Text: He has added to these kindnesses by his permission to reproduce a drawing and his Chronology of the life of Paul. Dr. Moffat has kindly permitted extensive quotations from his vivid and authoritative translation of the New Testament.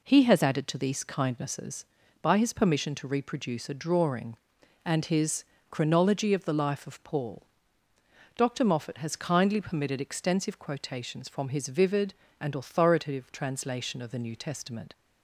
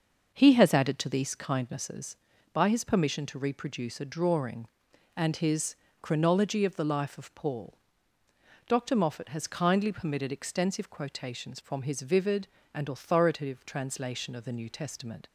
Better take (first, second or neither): first